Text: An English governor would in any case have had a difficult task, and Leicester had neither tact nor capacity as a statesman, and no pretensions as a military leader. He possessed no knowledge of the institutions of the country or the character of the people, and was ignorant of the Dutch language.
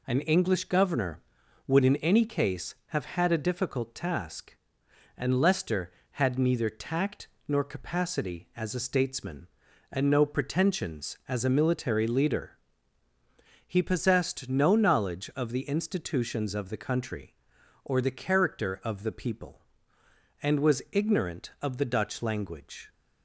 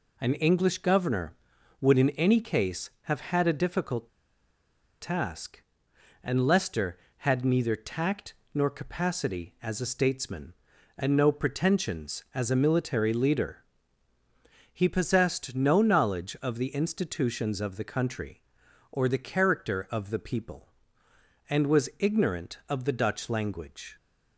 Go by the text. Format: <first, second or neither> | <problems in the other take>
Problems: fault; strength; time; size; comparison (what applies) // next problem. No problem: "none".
first | pauses between "difficult" and "task"; noticeable; at 4.0 s; 0.91 s long // pauses between "tact" and "nor"; slight; at 8.3 s; 0.20 s long; slight in the first